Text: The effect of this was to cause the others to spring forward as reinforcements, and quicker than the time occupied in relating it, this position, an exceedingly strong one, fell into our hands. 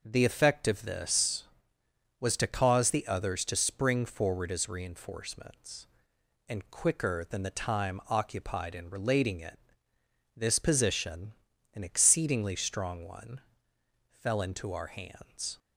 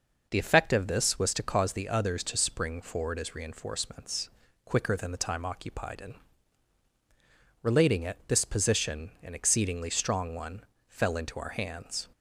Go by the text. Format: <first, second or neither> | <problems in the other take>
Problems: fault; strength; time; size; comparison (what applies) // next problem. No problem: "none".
first | skips "and"; at 4.4 s // pauses between "in" and "relating"; strong; at 6.1 s; 1.4 s long